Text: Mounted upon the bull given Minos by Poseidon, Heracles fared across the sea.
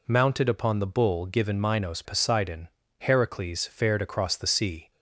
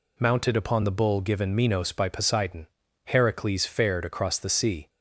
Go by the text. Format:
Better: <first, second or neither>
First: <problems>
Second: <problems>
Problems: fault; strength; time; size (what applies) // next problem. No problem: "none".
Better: second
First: skips "by"; at 2.0 s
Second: none